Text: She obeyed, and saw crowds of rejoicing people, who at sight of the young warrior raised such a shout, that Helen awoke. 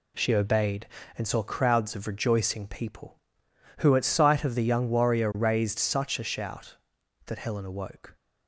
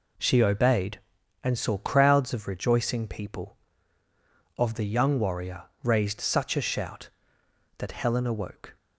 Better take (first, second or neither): first